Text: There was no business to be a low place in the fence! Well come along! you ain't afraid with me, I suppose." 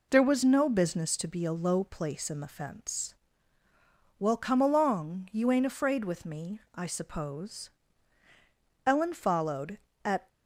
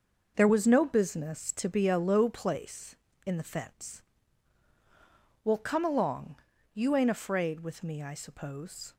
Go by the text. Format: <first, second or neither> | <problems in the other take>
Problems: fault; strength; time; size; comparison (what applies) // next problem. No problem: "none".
second | goes on to say "Ellen followed at"; from 8.8 s on; 1.4 s long